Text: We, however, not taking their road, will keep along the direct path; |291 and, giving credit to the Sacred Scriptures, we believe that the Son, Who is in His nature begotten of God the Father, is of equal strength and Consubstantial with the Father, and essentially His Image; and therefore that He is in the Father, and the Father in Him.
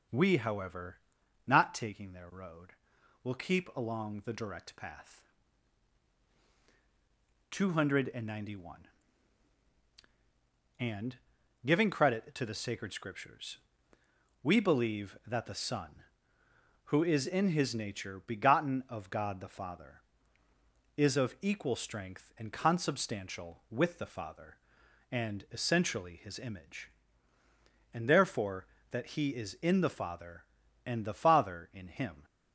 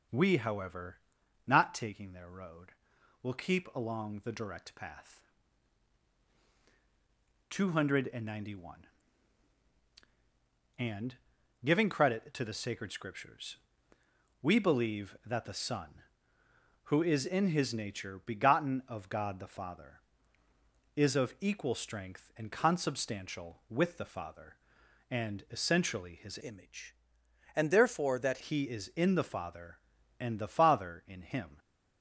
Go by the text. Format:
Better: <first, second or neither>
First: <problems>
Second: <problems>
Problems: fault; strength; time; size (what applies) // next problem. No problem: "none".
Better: first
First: none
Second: changes voice from "Image" to "that"; from 26.4 to 28.3 s; 1.9 s long